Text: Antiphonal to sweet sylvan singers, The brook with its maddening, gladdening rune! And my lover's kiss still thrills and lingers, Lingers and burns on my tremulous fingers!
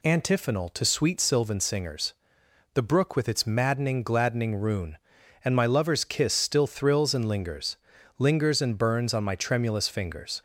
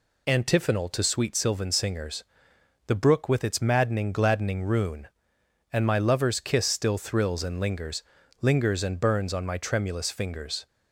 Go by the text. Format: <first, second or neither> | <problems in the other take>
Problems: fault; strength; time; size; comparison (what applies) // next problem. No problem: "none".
neither | none